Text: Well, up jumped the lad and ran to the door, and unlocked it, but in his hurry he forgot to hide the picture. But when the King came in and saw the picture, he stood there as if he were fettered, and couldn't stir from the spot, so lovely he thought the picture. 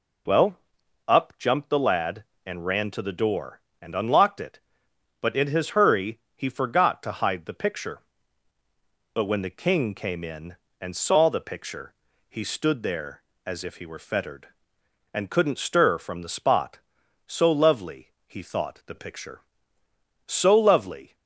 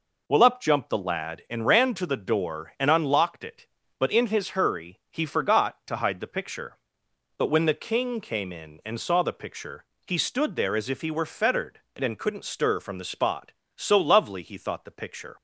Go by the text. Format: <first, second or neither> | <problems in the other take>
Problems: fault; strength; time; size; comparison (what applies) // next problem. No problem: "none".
second | pauses between "hurry" and "he"; slight; at 6.1 s; 0.16 s long // pauses between "lovely" and "he"; slight; at 18.0 s; 0.18 s long // goes on to say "So lovely"; noticeable; from 20.2 s on; 0.88 s long